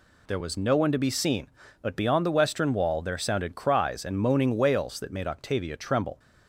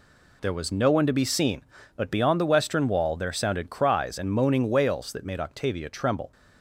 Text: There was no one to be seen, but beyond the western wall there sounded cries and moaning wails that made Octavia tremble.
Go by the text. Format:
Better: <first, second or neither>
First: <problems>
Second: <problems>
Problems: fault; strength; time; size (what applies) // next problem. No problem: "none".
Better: first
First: none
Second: gets quieter; strong; throughout; 9 dB